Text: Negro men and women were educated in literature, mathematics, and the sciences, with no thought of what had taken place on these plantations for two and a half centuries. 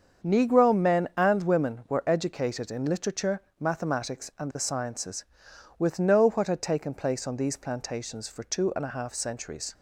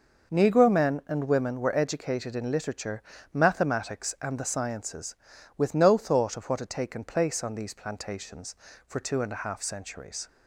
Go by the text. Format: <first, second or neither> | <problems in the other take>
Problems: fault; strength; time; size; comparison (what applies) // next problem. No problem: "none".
second | starts louder than the rest; strong; until 1.3 s; 7 dB // skips "thought of"; at 6.2 s